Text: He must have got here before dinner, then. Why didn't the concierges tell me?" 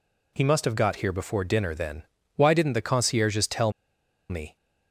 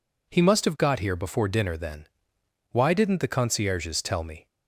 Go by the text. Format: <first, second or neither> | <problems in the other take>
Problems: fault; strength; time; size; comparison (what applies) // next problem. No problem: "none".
second | pauses between "tell" and "me"; noticeable; at 3.7 s; 0.59 s long